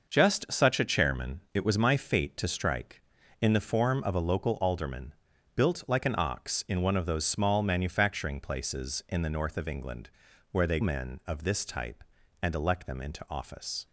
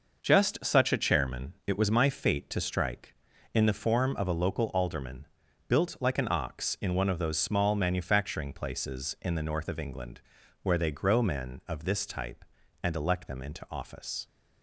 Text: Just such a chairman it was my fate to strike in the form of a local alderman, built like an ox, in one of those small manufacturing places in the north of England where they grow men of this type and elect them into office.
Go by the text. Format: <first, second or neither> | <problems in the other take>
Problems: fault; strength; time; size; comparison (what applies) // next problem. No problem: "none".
second | pauses between "England" and "where"; at 10.0 s; 0.42 s long; also in the second // skips "grow"; at 10.8 s